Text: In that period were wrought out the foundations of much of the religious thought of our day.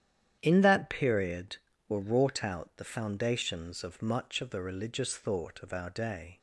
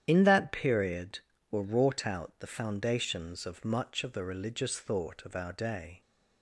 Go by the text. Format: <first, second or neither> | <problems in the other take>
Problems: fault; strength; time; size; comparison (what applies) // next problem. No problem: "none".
first | loses the start of "In"; at 0.0 s; 55 ms // starts louder than the rest; strong; until 1.0 s; 10 dB; strong in the first